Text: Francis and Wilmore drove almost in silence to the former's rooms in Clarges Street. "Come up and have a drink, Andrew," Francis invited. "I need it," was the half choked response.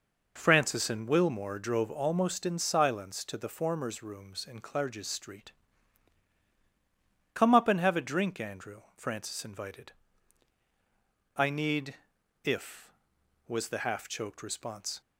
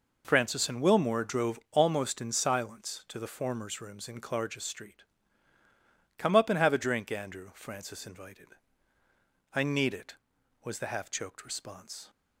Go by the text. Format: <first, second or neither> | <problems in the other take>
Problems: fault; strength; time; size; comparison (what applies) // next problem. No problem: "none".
second | says "if" for "it"; at 12.4 s